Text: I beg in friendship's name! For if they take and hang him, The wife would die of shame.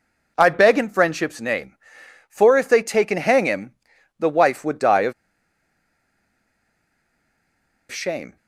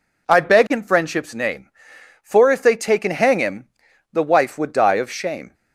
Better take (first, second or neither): second